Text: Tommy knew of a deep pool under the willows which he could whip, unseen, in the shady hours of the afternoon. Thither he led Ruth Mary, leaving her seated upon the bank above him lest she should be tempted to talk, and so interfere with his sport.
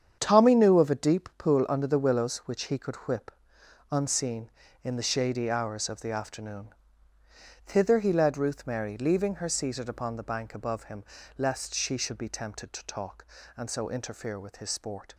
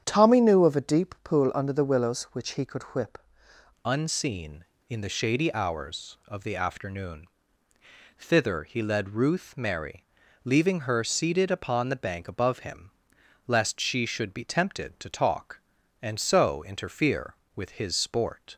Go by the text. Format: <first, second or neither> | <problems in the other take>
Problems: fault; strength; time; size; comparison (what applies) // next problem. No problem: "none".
first | starts louder than the rest; strong; until 1.0 s; 8.5 dB; strong in the first // changes voice at "unseen"; from 3.8 s on; 14.7 s long // pauses between "him" and "lest"; noticeable; at 12.8 s; 0.56 s long; slight in the first